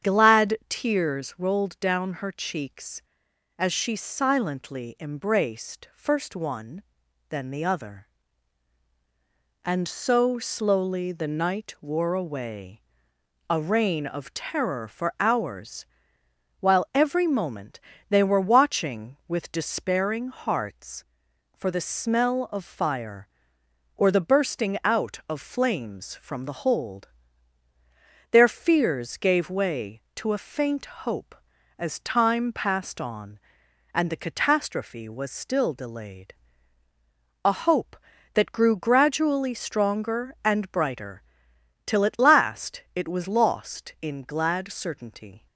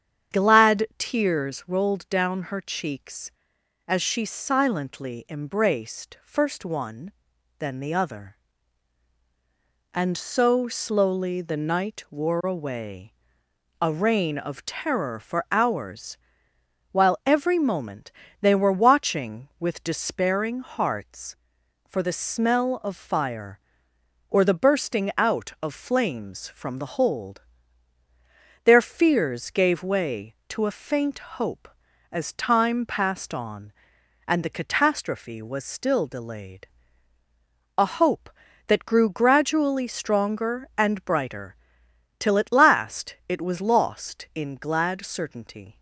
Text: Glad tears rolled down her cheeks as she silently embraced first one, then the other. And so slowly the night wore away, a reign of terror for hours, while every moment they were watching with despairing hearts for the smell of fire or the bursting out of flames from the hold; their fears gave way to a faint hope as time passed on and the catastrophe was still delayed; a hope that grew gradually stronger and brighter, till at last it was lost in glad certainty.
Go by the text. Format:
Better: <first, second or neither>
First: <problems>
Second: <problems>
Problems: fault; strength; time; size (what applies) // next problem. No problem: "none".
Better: neither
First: starts louder than the rest; strong; until 1.1 s; 8.5 dB // pauses between "moment" and "they"; slight; at 17.8 s; 0.28 s long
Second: starts louder than the rest; strong; until 1.4 s; 8.5 dB // pauses between "moment" and "they"; slight; at 18.1 s; 0.28 s long